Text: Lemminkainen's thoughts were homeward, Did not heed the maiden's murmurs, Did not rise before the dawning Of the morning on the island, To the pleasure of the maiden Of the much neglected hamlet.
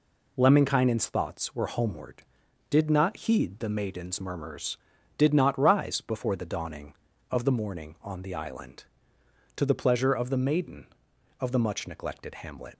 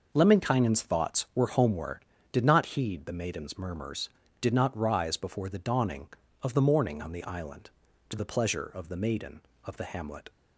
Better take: first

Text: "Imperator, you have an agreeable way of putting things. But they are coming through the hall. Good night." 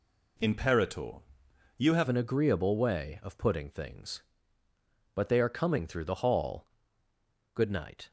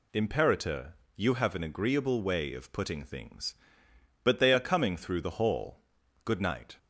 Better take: second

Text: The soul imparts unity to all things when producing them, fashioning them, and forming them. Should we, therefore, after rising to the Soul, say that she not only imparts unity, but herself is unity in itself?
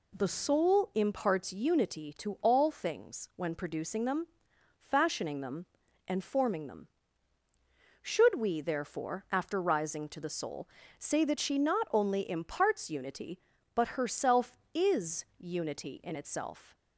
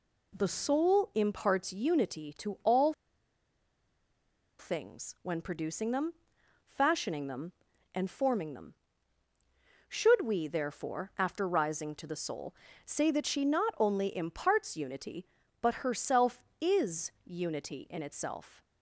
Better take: first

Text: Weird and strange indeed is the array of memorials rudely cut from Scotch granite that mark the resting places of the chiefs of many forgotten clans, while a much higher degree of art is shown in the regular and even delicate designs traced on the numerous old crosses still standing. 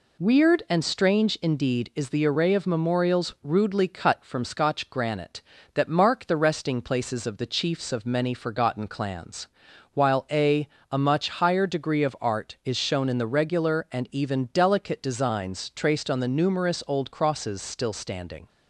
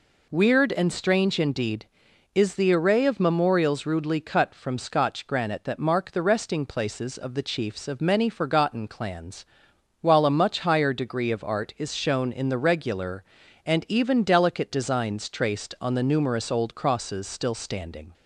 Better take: second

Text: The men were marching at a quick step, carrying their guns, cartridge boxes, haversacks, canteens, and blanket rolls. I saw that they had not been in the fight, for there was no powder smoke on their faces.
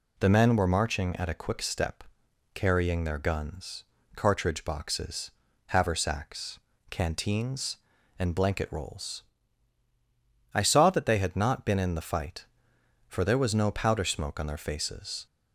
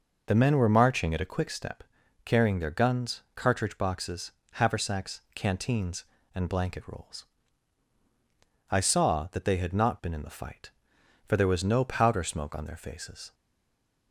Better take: first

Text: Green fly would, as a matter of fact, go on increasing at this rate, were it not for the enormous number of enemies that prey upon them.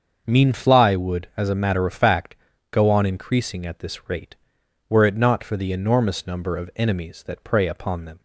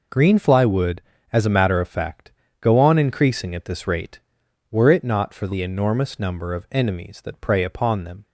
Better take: second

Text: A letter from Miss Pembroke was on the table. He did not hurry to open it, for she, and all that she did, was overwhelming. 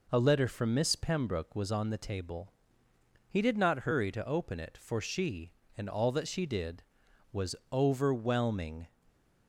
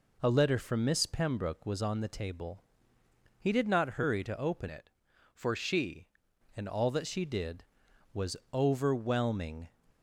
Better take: first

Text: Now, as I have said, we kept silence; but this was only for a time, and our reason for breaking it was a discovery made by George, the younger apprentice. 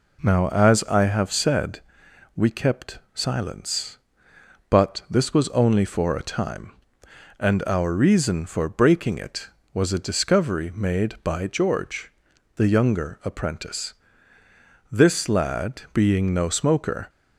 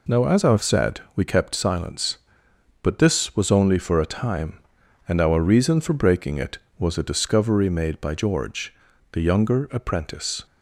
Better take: second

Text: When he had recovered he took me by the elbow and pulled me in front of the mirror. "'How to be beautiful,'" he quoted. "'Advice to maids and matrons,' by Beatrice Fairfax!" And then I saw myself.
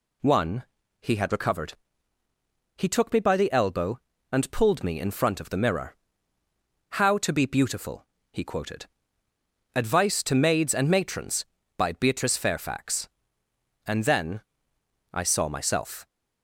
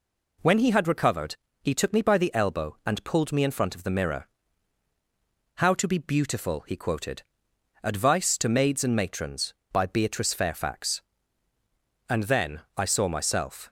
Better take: second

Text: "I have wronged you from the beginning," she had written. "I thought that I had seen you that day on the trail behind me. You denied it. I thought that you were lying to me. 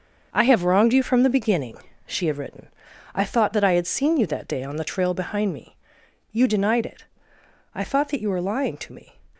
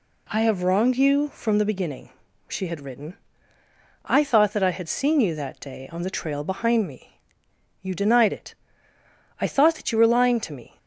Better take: second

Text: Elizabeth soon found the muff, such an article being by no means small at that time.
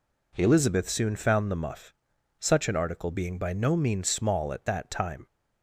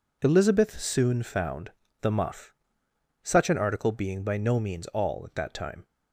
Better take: first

